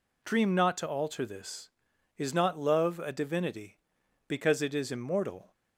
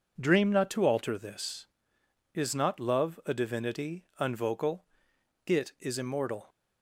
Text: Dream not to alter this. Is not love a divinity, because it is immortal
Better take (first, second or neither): first